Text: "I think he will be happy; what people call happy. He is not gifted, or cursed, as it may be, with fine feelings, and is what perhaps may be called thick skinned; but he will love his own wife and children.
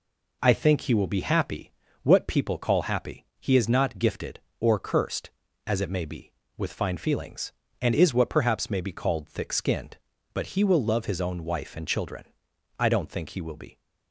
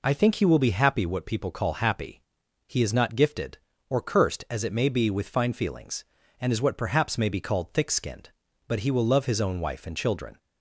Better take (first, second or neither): second